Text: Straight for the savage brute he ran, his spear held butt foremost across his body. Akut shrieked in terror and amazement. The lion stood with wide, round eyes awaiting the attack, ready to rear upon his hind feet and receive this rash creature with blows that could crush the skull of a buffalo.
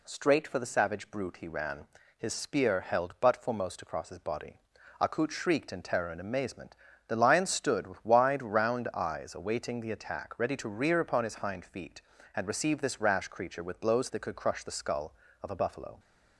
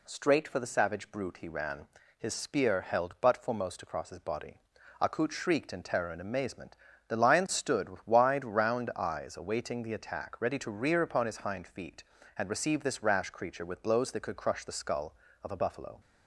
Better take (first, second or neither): neither